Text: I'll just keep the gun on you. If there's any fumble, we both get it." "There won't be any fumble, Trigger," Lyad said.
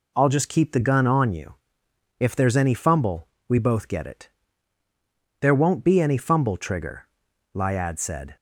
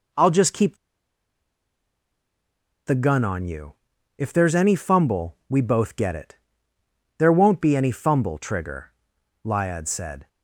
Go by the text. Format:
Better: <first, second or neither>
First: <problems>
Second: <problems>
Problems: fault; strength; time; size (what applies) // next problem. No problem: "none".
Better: first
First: none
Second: pauses between "keep" and "the"; strong; at 0.7 s; 2.1 s long